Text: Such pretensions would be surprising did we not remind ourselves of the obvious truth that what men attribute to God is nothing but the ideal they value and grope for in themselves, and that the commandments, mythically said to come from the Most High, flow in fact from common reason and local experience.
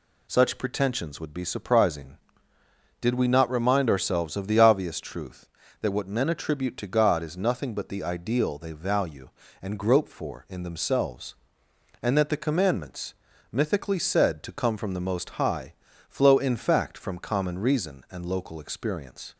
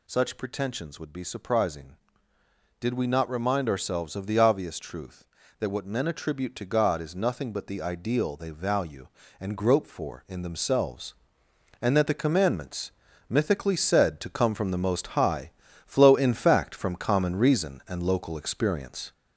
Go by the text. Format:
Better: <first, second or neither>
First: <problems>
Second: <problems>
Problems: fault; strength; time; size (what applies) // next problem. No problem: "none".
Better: first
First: none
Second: gets louder; noticeable; throughout; 4 dB